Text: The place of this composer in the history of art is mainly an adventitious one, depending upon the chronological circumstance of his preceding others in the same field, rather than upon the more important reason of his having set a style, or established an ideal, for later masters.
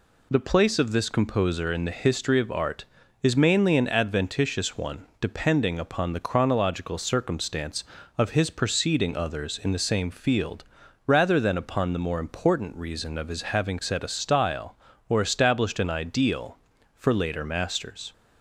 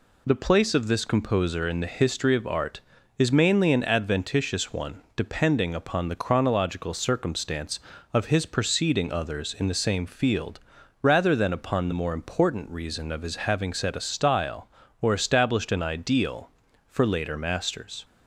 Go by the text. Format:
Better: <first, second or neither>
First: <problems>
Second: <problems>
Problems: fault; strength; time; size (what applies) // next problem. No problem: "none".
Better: neither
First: none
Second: none